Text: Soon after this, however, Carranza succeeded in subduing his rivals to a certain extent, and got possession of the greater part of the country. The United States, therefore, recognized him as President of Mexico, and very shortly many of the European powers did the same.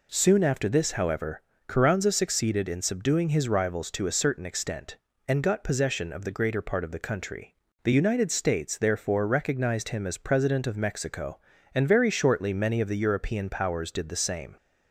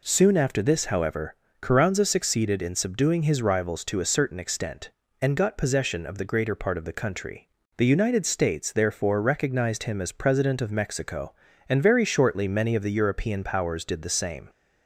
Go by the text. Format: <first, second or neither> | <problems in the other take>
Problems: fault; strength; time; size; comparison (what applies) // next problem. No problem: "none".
neither | none